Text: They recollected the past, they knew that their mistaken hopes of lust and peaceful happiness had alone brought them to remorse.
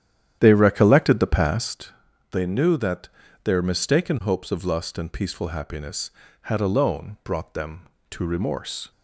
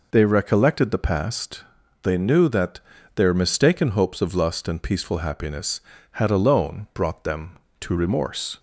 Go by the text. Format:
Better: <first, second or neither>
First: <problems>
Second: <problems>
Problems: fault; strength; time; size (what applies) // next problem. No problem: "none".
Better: second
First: starts louder than the rest; strong; until 1.7 s; 10 dB // pauses between "that" and "their"; at 3.0 s; 0.38 s long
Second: pauses between "that" and "their"; at 2.7 s; 0.38 s long